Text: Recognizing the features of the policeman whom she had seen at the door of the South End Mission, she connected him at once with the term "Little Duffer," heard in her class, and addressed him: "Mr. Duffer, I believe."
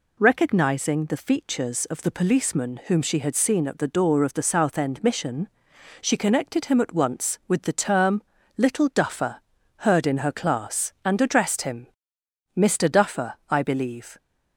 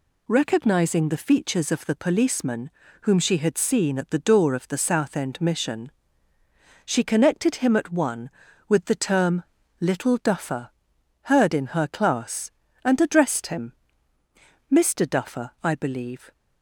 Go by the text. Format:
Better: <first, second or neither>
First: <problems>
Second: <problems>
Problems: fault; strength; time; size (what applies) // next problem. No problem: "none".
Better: first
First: pauses between "term" and "Little"; slight; at 8.2 s; 0.36 s long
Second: pauses between "policeman" and "whom"; slight; at 2.6 s; 0.32 s long // says "one" for "once"; at 7.9 s // pauses between "term" and "Little"; at 9.4 s; 0.38 s long